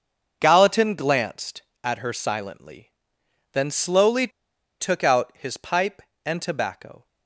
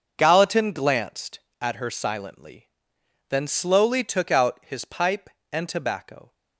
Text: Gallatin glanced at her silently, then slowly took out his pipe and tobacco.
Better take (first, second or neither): second